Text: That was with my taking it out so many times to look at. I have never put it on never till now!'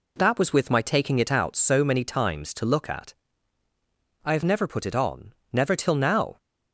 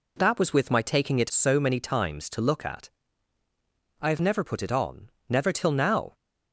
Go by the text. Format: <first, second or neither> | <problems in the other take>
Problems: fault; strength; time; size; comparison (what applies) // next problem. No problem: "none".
first | skips "out"; at 1.3 s // pauses between "on" and "never"; slight; at 5.1 s; 0.18 s long; slight in the first